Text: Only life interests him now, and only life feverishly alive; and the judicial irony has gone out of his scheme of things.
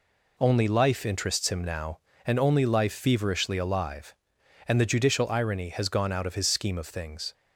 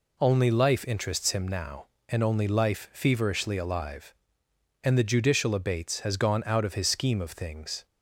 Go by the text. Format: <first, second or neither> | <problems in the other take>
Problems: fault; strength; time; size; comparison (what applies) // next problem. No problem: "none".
first | says "abates" for "irony"; at 5.5 s